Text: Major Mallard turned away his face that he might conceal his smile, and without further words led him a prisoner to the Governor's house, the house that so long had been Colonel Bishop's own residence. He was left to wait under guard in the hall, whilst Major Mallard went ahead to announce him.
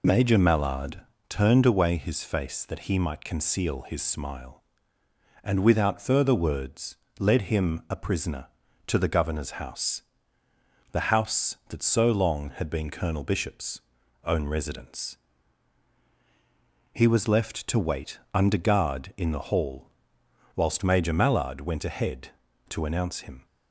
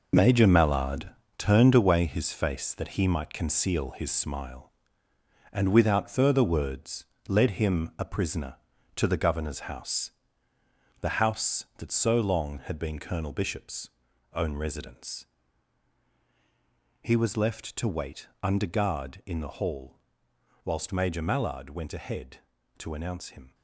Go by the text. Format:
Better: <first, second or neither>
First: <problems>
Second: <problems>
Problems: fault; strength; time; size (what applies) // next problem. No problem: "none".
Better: first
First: pauses between "Mallard" and "turned"; slight; at 0.9 s; 0.32 s long // pauses between "words" and "led"; slight; at 6.9 s; 0.22 s long // pauses between "Bishop's" and "own"; at 13.7 s; 0.44 s long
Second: gets quieter; strong; throughout; 9.5 dB // pauses between "Mallard" and "turned"; slight; at 1.0 s; 0.32 s long // pauses between "words" and "led"; slight; at 7.0 s; 0.22 s long // pauses between "Bishop's" and "own"; at 13.8 s; 0.44 s long